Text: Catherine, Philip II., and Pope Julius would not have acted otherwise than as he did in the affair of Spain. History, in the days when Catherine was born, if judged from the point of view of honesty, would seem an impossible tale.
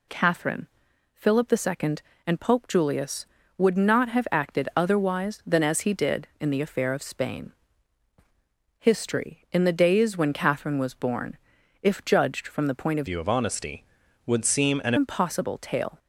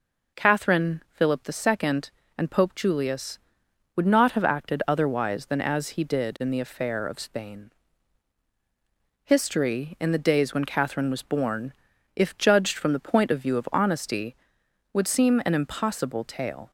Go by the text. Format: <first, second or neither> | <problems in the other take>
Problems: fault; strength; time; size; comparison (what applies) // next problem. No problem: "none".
second | changes voice from "view" to "an"; from 13.0 to 14.9 s; 1.9 s long